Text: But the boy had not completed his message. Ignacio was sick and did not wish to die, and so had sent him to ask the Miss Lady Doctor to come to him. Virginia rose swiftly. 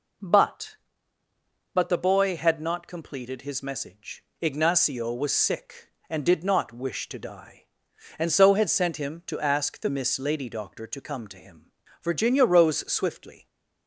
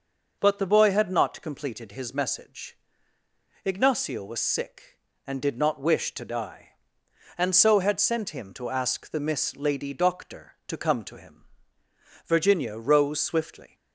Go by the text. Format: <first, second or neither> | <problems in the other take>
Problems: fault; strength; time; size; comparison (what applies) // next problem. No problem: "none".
second | says "But" twice; at 1.7 s